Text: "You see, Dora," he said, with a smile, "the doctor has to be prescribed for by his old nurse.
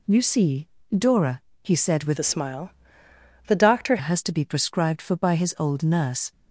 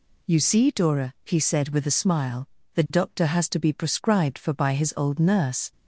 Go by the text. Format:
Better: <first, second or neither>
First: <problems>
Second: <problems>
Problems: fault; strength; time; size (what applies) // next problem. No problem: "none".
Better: second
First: changes voice from "a" to "doctor"; from 2.1 to 3.9 s; 1.8 s long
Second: none